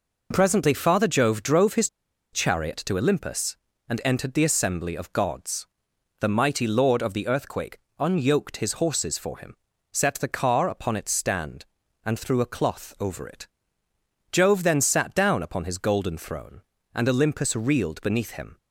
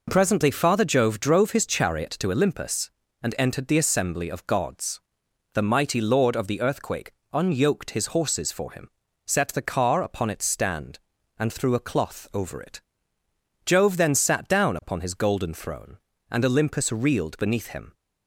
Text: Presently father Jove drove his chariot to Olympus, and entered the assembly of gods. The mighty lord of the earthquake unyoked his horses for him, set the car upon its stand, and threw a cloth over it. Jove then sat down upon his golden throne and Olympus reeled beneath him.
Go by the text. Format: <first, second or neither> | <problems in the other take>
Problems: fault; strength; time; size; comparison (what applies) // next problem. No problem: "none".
second | pauses between "his" and "chariot"; at 1.8 s; 0.43 s long // pauses between "earthquake" and "unyoked"; slight; at 7.7 s; 0.20 s long; slight in the second